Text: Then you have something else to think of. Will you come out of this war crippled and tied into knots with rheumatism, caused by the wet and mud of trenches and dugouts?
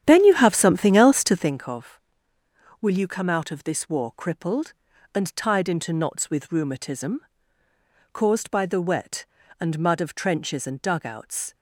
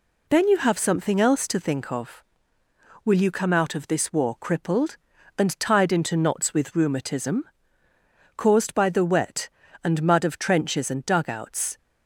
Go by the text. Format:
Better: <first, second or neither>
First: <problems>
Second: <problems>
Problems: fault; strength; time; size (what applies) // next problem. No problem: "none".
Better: second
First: starts louder than the rest; strong; until 1.6 s; 10 dB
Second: none